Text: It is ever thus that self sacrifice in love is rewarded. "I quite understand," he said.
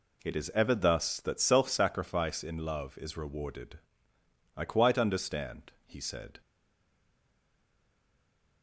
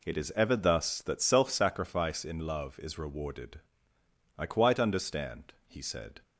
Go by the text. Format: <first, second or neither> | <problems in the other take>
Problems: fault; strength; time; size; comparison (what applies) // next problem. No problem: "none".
second | stays silent after the last word; from 6.4 s on; 2.2 s long